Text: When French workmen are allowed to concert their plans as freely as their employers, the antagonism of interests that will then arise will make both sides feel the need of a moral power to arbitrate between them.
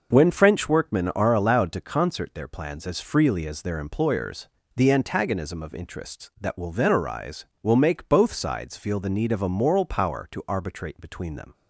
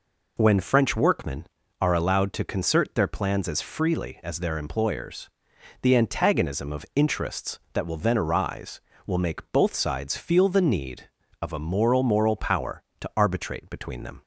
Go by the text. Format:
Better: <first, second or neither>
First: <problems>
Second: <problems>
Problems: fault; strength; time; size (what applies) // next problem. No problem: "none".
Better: first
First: none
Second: says "moral" twice; at 12.0 s